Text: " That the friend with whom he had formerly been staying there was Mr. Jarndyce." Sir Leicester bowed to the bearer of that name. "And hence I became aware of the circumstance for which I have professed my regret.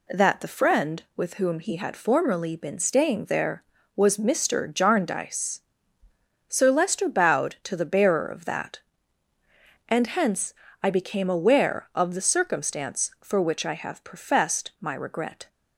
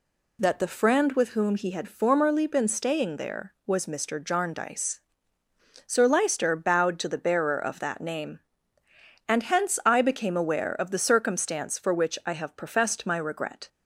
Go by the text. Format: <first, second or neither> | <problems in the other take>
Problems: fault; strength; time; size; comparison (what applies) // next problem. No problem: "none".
second | skips "name"; at 9.3 s // pauses between "hence" and "I"; slight; at 10.5 s; 0.28 s long